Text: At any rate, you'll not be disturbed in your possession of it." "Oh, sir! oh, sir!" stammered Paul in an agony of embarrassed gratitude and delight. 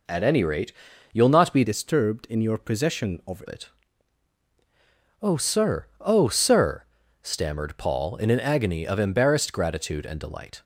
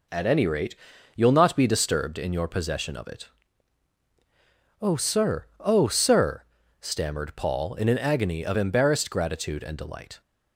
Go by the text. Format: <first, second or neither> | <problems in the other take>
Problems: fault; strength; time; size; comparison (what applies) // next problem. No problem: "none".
second | changes voice from "disturbed" to "of"; from 1.6 to 3.4 s; 1.8 s long